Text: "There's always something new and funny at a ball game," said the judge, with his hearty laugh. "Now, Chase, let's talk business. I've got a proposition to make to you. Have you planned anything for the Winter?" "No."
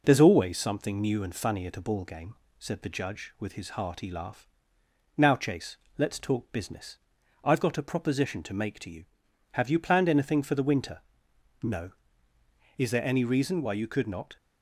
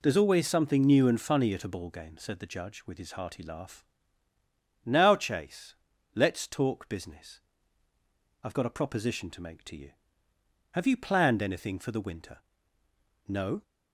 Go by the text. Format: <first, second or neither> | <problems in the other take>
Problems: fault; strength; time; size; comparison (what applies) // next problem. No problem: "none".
second | goes on to say "Is there any reason why you could not"; from 12.7 s on; 1.5 s long